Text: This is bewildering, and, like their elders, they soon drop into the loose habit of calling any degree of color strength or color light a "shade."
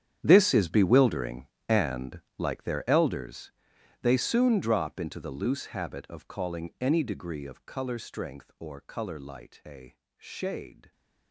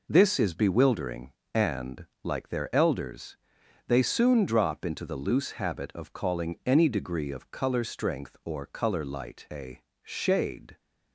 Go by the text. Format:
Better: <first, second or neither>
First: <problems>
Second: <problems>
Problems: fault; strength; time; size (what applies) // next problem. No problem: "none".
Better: second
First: gets quieter; strong; throughout; 17 dB // pauses between "a" and "shade"; slight; at 9.9 s; 0.22 s long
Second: pauses between "a" and "shade"; slight; at 9.8 s; 0.22 s long